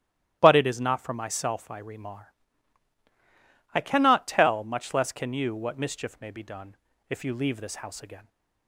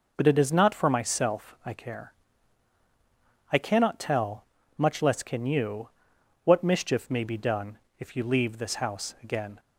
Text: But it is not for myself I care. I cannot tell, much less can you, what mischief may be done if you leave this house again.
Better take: second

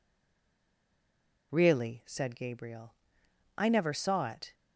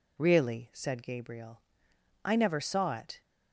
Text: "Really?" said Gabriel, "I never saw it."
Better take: second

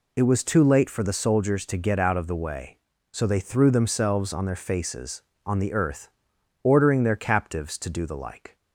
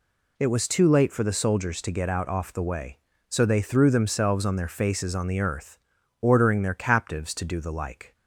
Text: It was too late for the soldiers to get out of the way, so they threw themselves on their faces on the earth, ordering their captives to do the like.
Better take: first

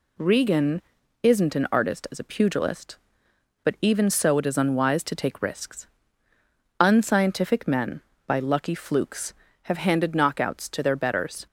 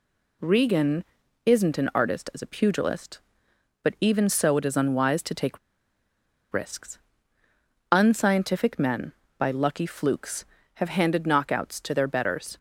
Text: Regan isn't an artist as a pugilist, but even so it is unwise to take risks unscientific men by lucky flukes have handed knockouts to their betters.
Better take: first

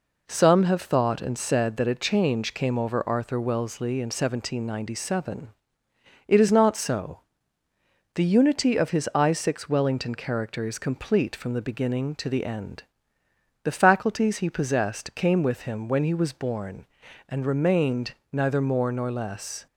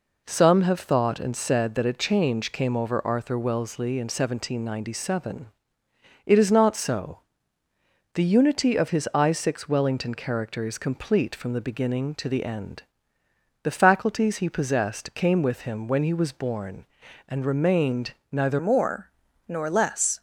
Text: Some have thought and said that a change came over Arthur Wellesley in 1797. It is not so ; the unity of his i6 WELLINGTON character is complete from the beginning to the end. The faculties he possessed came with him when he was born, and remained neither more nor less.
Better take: first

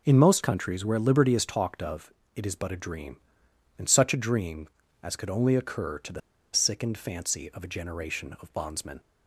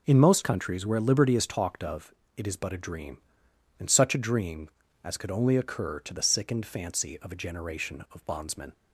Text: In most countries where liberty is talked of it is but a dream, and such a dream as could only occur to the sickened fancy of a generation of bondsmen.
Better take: second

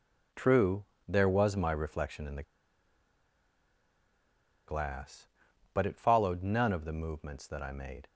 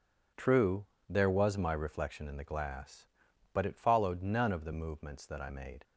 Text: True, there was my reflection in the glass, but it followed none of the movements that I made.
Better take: second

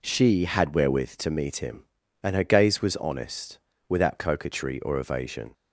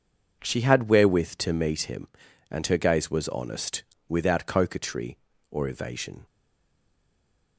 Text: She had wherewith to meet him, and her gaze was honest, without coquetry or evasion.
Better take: first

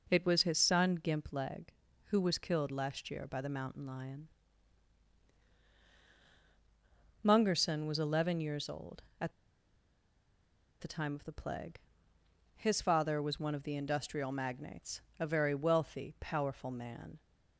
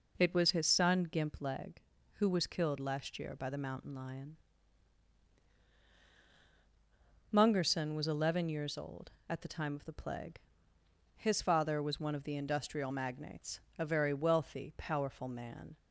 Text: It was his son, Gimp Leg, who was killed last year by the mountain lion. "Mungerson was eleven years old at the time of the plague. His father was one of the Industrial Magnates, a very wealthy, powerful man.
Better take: second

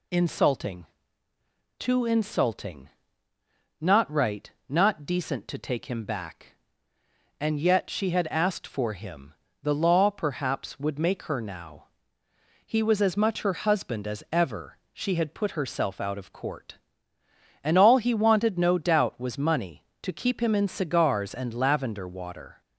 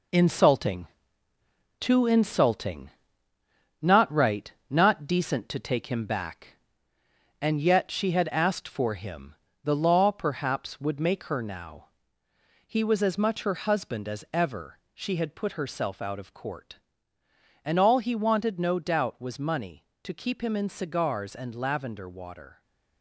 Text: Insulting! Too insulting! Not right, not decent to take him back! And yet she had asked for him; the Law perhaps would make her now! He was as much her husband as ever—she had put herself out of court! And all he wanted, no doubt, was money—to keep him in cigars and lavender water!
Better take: first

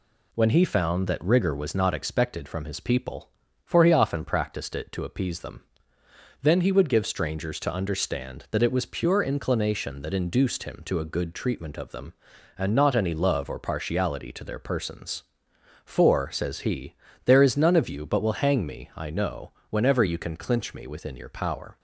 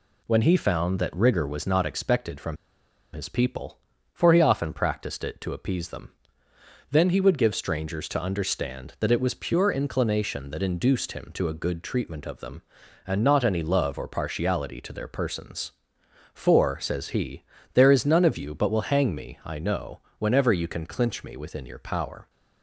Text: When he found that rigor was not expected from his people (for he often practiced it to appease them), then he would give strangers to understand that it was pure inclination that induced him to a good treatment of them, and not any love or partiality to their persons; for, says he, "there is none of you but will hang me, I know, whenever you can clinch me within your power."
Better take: first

